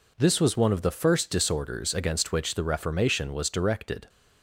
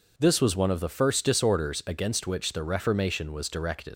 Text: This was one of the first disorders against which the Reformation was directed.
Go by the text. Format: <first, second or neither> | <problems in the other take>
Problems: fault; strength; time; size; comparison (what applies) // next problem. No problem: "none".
first | leaves "directed" unfinished; at 3.9 s; 115 ms